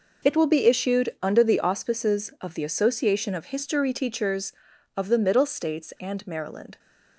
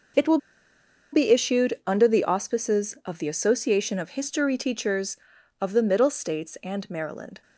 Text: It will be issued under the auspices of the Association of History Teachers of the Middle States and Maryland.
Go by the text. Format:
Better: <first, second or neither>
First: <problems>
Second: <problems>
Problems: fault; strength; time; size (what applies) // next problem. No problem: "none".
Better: first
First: none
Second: pauses between "will" and "be"; noticeable; at 0.3 s; 0.75 s long